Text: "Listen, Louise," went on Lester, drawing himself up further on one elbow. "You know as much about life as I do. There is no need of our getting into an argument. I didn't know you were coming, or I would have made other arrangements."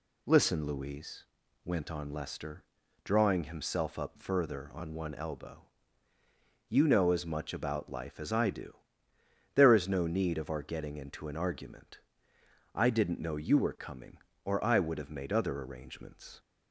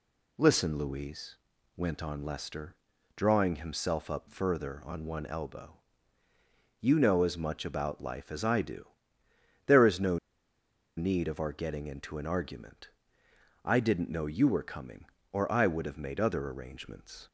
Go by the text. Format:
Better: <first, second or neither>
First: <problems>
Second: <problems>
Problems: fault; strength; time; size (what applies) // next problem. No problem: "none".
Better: first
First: none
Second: pauses between "no" and "need"; noticeable; at 10.1 s; 0.79 s long